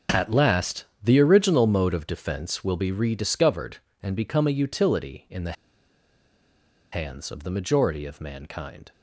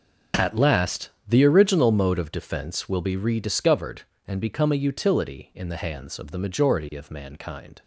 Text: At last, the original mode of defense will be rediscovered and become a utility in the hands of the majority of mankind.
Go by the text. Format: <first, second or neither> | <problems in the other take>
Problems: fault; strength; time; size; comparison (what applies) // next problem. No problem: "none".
second | pauses between "the" and "hands"; strong; at 5.5 s; 1.3 s long